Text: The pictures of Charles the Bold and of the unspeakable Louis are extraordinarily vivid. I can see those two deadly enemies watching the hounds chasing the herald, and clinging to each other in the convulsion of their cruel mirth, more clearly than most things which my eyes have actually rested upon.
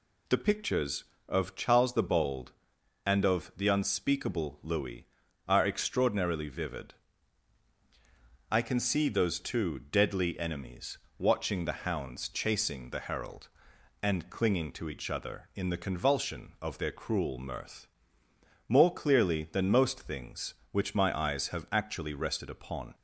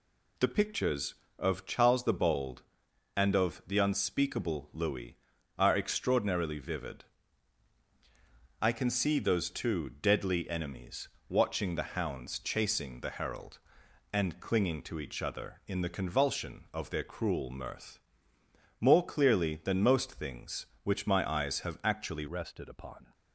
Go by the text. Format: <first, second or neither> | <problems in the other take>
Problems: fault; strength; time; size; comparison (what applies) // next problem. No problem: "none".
first | pauses between "enemies" and "watching"; slight; at 11.0 s; 0.18 s long; slight in the first // changes voice at "rested"; from 22.2 s on; 0.9 s long